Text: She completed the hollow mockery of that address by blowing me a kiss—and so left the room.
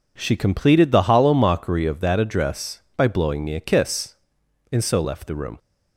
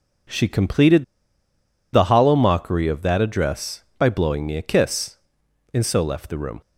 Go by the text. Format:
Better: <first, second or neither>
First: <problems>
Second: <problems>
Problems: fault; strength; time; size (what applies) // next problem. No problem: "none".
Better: first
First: none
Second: pauses between "completed" and "the"; noticeable; at 1.0 s; 0.90 s long